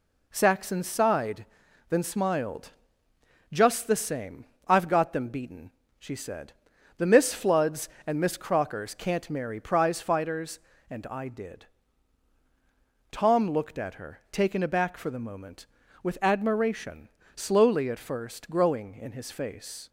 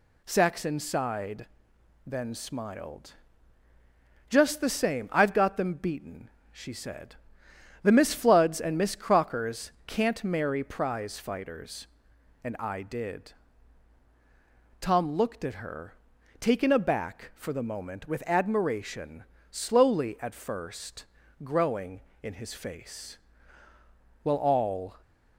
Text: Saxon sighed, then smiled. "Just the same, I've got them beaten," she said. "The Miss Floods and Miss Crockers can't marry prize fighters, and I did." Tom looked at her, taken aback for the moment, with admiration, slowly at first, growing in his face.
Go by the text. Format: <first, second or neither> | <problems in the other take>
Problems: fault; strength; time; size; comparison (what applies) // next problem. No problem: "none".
first | pauses between "Crockers" and "can't"; slight; at 9.7 s; 0.16 s long // goes on to say "Well all"; noticeable; from 24.2 s on; 0.78 s long